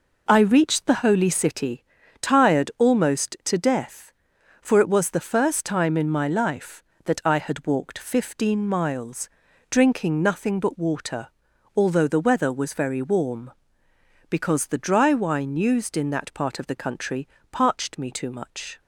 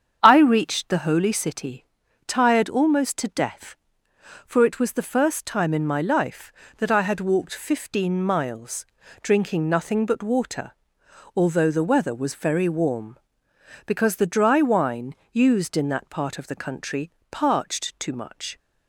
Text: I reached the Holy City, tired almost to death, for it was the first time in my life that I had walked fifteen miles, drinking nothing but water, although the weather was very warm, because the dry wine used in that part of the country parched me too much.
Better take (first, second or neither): first